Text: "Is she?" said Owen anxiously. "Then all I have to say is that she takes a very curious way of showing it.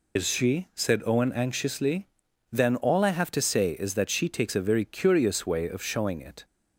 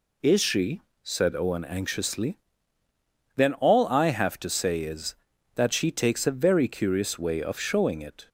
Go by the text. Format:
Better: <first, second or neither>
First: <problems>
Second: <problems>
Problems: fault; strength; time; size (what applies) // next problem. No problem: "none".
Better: second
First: loses the start of "Is"; at 0.1 s; 90 ms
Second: none